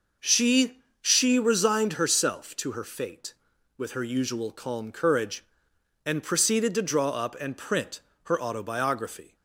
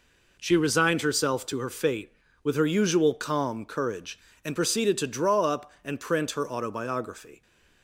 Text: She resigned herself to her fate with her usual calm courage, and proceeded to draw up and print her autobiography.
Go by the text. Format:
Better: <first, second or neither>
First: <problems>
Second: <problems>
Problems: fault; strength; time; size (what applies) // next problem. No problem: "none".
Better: second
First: says "She" twice; at 1.0 s // pauses between "print" and "her"; slight; at 7.9 s; 0.24 s long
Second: none